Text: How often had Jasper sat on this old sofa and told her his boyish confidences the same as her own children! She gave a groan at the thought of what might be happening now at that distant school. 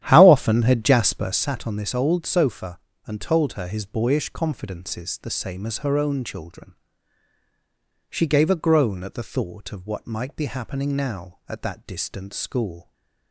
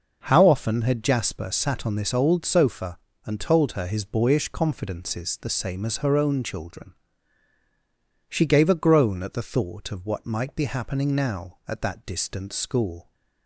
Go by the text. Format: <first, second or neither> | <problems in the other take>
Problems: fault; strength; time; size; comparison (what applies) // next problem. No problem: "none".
second | starts louder than the rest; strong; until 1.5 s; 11 dB